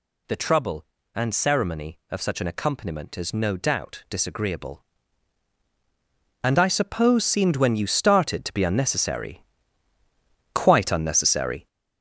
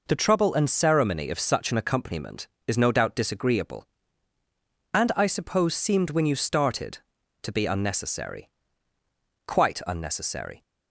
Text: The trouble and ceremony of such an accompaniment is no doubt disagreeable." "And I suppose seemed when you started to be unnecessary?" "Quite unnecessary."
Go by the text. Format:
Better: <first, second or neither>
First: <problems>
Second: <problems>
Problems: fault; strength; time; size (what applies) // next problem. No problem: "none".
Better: second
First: gets louder; strong; throughout; 8 dB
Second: none